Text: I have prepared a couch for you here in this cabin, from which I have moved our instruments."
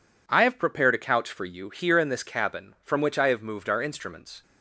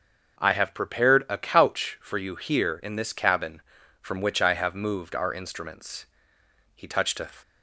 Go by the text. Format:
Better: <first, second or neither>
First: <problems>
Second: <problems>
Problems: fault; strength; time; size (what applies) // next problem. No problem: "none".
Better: first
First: none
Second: starts louder than the rest; noticeable; until 1.4 s; 6 dB // goes on to say "He touched a"; from 6.7 s on; 0.54 s long